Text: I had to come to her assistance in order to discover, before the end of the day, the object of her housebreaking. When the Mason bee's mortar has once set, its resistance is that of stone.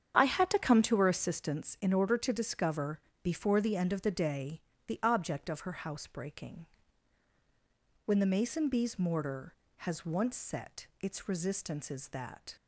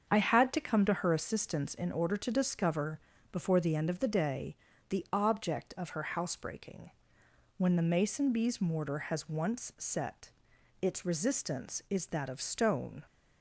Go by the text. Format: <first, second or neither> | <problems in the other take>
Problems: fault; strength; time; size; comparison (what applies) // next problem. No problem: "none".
second | starts louder than the rest; strong; until 1.2 s; 8 dB; also in the second // stops before "of stone"; at 12.5 s